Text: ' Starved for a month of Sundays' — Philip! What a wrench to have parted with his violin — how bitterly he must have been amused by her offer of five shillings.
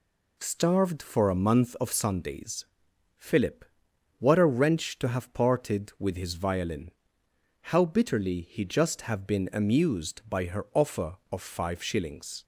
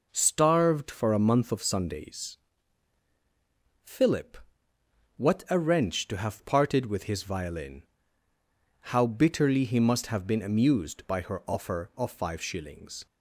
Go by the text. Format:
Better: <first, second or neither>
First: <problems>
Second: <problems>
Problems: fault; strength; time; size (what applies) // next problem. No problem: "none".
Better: second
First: says "just" for "must"; at 8.6 s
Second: none